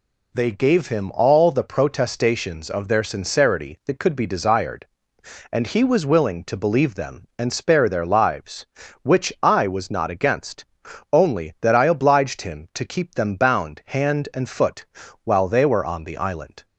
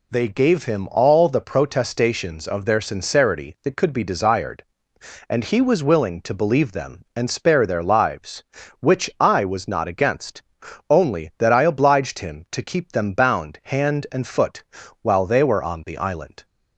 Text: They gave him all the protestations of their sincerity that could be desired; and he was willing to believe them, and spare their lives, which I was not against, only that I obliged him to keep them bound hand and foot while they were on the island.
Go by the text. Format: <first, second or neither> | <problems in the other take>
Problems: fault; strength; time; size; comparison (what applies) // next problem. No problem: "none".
neither | pauses between "foot" and "while"; the same in both